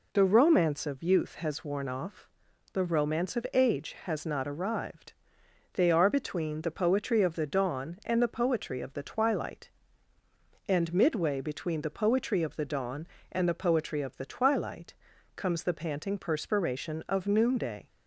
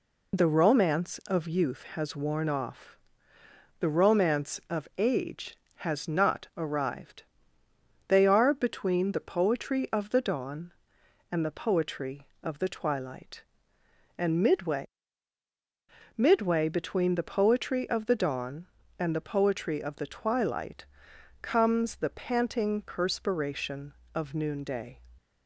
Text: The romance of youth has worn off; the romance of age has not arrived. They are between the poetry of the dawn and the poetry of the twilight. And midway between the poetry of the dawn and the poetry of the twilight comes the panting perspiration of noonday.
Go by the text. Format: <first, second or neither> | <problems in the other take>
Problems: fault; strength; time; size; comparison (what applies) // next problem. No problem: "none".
first | says "midway" twice; at 16.1 s // pauses between "twilight" and "comes"; noticeable; at 20.8 s; 0.58 s long; also in the first